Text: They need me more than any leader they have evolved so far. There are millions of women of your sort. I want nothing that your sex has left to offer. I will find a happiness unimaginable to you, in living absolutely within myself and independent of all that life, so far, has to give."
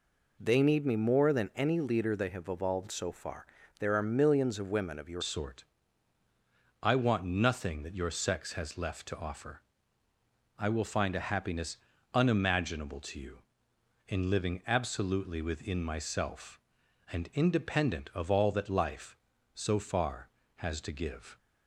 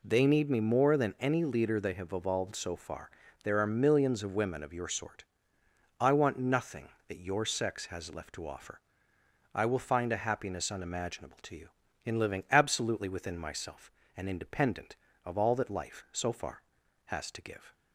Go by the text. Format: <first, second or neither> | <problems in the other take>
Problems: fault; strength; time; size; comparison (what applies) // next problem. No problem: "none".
second | changes voice at "sort"; from 5.2 s on; 16.1 s long // pauses between "happiness" and "unimaginable"; at 11.7 s; 0.38 s long